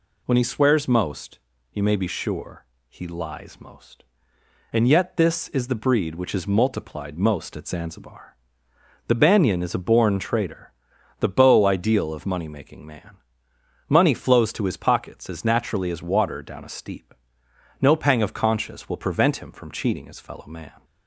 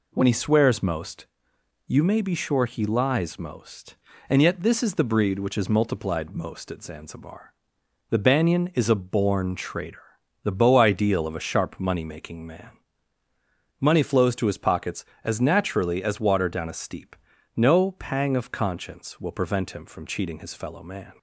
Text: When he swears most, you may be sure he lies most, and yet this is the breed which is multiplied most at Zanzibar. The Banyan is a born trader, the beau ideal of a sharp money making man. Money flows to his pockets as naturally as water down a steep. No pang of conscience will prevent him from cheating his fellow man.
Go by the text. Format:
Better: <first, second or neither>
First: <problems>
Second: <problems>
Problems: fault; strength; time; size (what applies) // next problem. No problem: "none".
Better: second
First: pauses between "sure" and "he"; slight; at 2.6 s; 0.24 s long // skips "a sharp"; at 12.2 s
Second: none